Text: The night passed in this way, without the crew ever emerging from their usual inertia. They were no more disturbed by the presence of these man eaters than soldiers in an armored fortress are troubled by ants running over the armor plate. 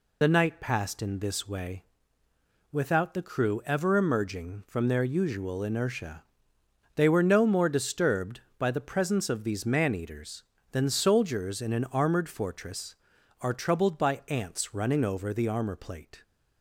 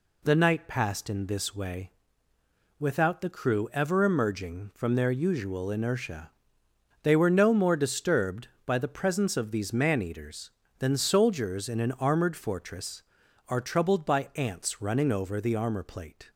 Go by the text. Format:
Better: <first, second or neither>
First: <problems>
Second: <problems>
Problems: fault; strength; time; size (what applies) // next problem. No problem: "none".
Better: second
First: loses the start of "The"; at 0.2 s; 50 ms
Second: none